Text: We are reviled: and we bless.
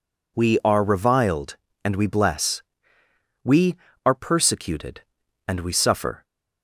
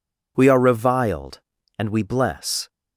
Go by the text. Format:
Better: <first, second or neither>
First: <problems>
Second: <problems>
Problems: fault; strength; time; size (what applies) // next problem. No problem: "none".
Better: second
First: goes on to say "We are persecuted and we suffer"; strong; from 3.4 s on; 2.8 s long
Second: none